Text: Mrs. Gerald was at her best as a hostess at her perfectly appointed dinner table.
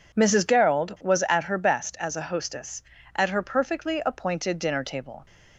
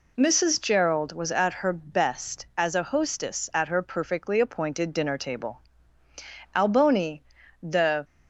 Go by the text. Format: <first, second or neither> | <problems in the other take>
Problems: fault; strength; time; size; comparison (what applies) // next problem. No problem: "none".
first | goes on to say "Alboni the"; from 6.5 s on; 1.5 s long